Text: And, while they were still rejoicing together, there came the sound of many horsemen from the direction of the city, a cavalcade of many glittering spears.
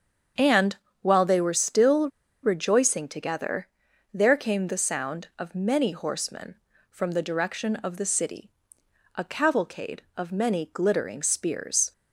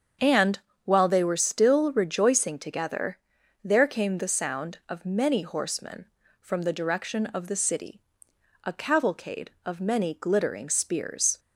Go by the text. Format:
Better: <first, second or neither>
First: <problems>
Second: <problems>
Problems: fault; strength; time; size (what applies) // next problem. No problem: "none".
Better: second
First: starts louder than the rest; strong; until 1.6 s; 7.5 dB // pauses between "still" and "rejoicing"; slight; at 2.0 s; 0.33 s long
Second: starts louder than the rest; strong; until 1.4 s; 7.5 dB